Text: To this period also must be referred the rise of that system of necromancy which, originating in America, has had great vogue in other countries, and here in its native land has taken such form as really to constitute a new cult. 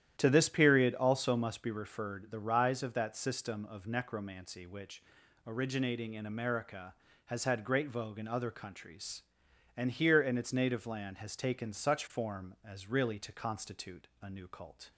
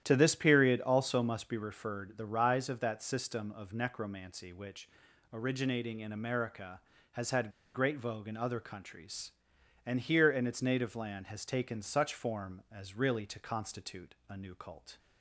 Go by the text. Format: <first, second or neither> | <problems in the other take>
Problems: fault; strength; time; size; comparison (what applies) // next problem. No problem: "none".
first | starts louder than the rest; strong; until 1.0 s; 11 dB; strong in the first // pauses between "had" and "great"; slight; at 7.5 s; 0.23 s long